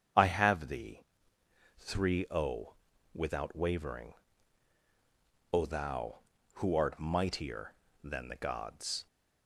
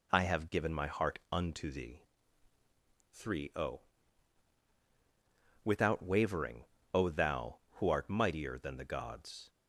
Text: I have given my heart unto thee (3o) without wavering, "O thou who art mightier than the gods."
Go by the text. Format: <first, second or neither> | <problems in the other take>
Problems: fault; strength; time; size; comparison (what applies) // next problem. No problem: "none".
second | starts louder than the rest; strong; until 1.9 s; 7.5 dB // skips "given my heart unto"; at 0.6 s